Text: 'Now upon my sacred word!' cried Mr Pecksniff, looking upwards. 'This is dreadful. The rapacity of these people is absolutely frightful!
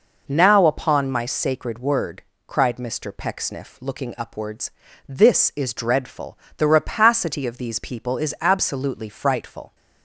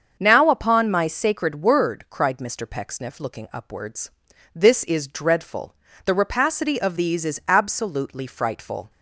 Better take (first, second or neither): first